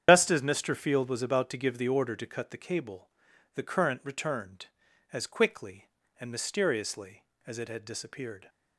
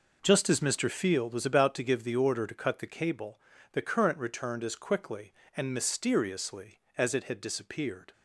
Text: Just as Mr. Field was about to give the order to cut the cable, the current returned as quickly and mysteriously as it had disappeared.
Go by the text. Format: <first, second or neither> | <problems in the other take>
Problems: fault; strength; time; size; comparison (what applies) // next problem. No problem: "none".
second | loses the start of "Just"; at 0.0 s; 80 ms // starts louder than the rest; strong; until 1.0 s; 9 dB